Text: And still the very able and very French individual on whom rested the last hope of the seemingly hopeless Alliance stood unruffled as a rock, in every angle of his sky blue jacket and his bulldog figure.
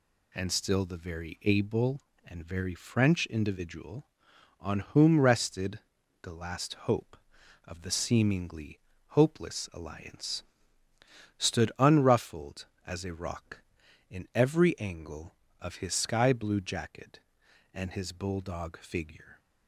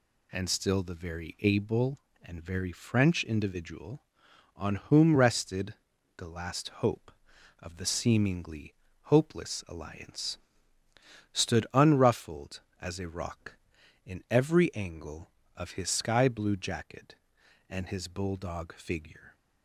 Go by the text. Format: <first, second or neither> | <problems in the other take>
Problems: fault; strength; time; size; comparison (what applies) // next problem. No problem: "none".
neither | pauses between "rested" and "the"; the same in both // pauses between "seemingly" and "hopeless"; slight; the same in both // pauses between "Alliance" and "stood"; noticeable; the same in both